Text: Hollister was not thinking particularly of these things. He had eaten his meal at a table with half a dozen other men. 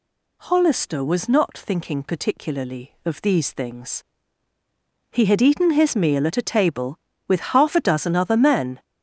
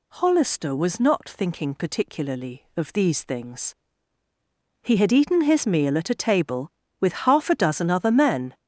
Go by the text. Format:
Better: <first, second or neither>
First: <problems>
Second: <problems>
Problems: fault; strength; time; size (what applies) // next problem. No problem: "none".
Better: neither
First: none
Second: none